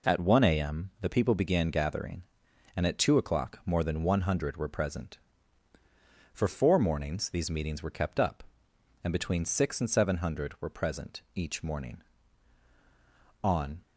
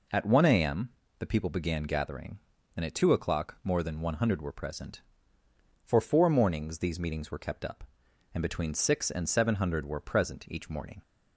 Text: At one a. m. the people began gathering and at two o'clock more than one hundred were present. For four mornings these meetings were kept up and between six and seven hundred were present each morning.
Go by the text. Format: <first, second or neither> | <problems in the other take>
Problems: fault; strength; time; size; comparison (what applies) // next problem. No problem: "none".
second | goes on to say "On"; slight; from 13.4 s on; 0.36 s long